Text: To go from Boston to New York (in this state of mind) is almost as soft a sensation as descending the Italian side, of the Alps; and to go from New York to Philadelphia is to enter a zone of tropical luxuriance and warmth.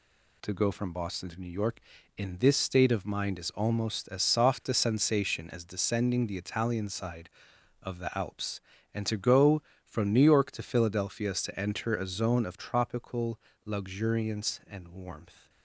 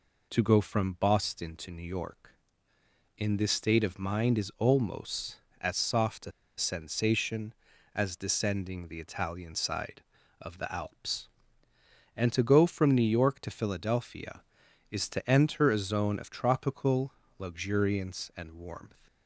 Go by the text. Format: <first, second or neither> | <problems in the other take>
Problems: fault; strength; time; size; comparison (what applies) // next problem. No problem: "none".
first | pauses between "a" and "sensation"; slight; at 6.3 s; 0.27 s long // pauses between "tropical" and "luxuriance"; slight; at 17.1 s; 0.26 s long; slight in the first